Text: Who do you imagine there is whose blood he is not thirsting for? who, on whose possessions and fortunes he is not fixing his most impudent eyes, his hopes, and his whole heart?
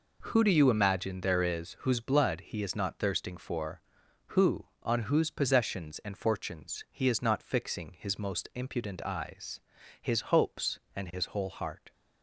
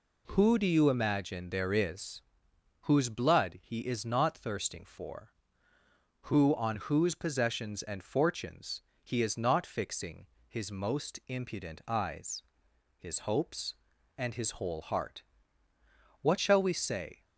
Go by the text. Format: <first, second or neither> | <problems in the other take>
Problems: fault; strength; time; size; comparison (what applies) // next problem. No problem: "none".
first | pauses between "is" and "whose"; noticeable; at 2.2 s; 0.60 s long // pauses between "fortunes" and "he"; slight; at 8.8 s; 0.20 s long // pauses between "fixing" and "his"; slight; at 10.2 s; 0.22 s long // goes on to say "What shall we say"; noticeable; from 16.2 s on; 1.0 s long